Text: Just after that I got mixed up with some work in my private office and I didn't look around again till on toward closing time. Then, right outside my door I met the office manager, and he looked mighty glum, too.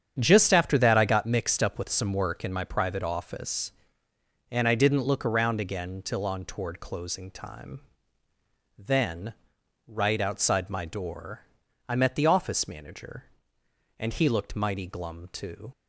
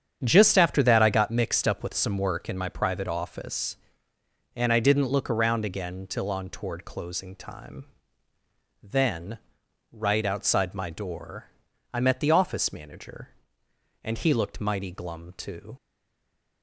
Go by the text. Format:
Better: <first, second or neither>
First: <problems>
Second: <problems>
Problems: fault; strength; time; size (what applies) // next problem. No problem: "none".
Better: first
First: starts louder than the rest; strong; until 1.1 s; 8.5 dB // pauses between "door" and "I"; noticeable; at 11.4 s; 0.46 s long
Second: starts louder than the rest; strong; until 1.2 s; 8.5 dB // pauses between "door" and "I"; noticeable; at 11.4 s; 0.46 s long // stays silent after the last word; slight; from 15.7 s on; 0.9 s long